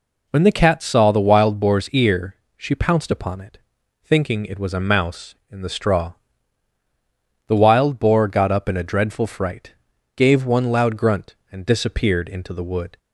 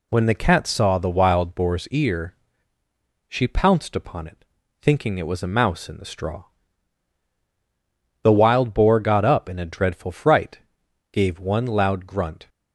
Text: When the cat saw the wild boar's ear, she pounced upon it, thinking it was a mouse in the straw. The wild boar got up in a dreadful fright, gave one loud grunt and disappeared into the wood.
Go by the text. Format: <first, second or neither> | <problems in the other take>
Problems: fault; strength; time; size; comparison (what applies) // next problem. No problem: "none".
first | stops before "and disappeared into the wood"; at 12.4 s